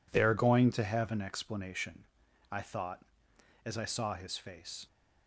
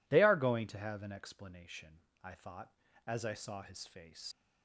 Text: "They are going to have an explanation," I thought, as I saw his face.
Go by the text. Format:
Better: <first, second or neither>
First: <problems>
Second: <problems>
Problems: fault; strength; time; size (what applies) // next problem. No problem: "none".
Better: first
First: none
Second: leaves "face" unfinished; at 4.3 s; 65 ms